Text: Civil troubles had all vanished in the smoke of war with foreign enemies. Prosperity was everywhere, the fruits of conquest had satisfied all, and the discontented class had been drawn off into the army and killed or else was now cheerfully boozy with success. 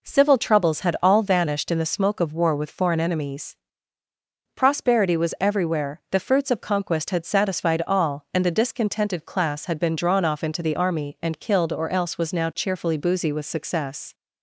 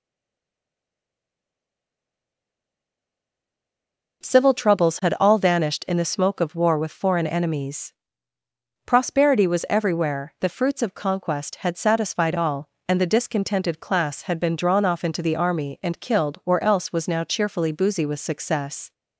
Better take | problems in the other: first | stays silent before the first word; strong; until 4.2 s; 4.2 s long

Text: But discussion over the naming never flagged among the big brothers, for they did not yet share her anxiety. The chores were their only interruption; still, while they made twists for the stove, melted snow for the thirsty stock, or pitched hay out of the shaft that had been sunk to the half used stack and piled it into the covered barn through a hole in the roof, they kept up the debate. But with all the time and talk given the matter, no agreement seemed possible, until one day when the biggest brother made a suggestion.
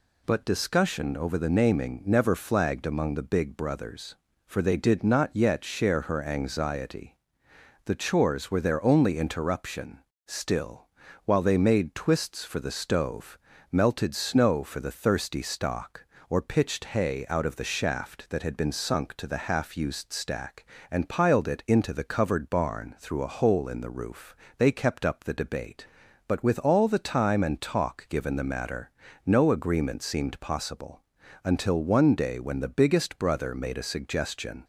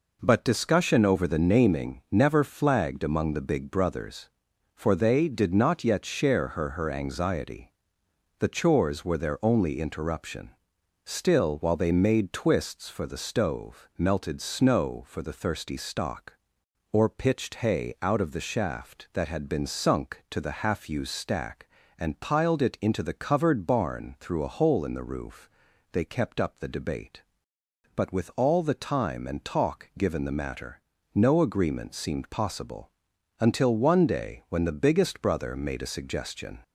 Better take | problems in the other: first | says "her" twice; at 6.7 s

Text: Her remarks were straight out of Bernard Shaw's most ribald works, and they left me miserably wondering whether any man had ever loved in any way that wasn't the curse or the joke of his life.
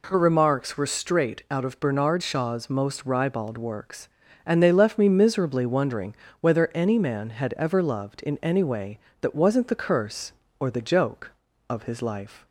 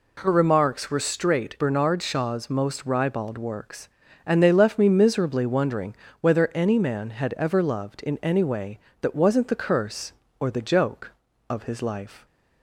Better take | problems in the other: first | skips "out of"; at 1.5 s // pauses between "wondering" and "whether"; slight; at 5.9 s; 0.28 s long; slight in the first

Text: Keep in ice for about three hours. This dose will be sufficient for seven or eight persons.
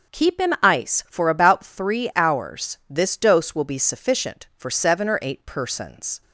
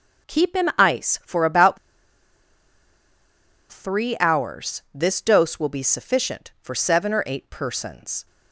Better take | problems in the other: first | pauses between "about" and "three"; strong; at 1.7 s; 1.9 s long

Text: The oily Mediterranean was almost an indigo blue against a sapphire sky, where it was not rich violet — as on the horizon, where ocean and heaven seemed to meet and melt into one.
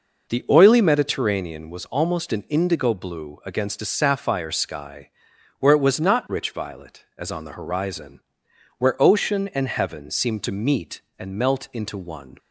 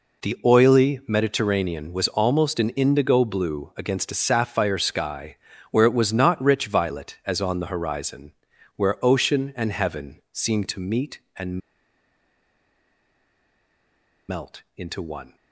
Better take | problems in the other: first | pauses between "and" and "melt"; strong; at 11.5 s; 2.6 s long

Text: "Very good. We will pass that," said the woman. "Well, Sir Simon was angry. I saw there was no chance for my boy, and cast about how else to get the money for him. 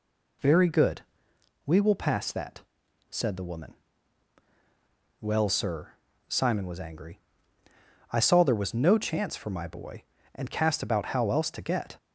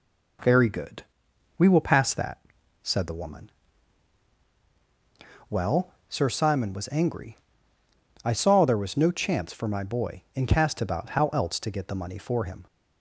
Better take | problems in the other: second | pauses between "Sir" and "Simon"; at 5.9 s; 0.38 s long // stops before "the money for him"; at 11.9 s

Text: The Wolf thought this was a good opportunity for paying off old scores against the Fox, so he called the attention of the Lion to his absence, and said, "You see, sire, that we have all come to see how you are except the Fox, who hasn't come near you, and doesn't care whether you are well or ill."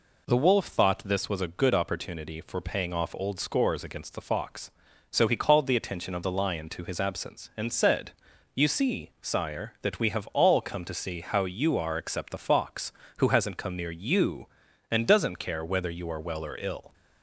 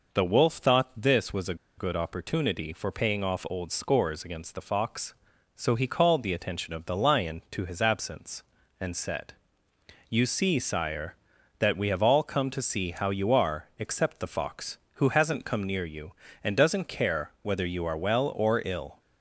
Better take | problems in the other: first | pauses between "a" and "good"; slight; at 1.5 s; 0.23 s long

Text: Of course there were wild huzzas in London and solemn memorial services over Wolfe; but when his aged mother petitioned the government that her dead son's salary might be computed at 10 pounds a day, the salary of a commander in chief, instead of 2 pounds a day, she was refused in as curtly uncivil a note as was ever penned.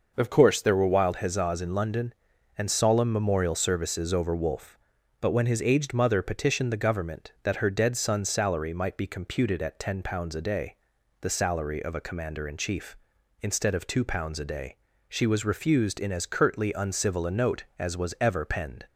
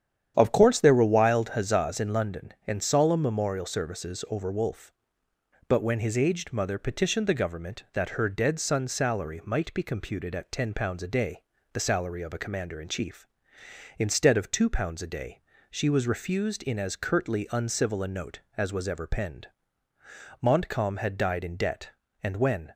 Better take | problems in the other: first | starts louder than the rest; strong; until 1.3 s; 9.5 dB // goes on to say "Montcalm had died in debt and when"; strong; from 20.4 s on; 2.3 s long

